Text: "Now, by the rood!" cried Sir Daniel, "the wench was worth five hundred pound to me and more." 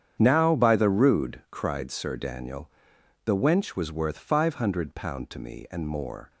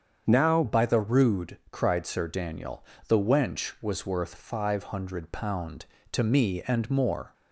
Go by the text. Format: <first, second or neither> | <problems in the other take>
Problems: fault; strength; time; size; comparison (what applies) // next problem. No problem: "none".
first | starts louder than the rest; strong; until 1.2 s; 7.5 dB; strong in the first // changes voice at "by"; from 0.6 s on; 6.7 s long